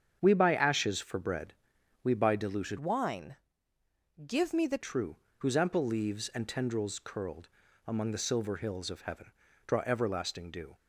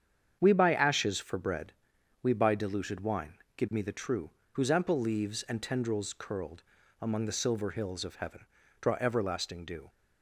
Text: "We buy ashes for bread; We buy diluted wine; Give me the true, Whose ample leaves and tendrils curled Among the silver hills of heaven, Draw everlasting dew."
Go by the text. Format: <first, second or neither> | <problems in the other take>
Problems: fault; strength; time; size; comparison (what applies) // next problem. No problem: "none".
second | starts louder than the rest; strong; until 1.2 s; 8 dB; strong in the second // changes voice from "wine" to "the"; from 2.7 to 4.7 s; 2.0 s long // pauses between "curled" and "Among"; at 7.4 s; 0.40 s long; also in the second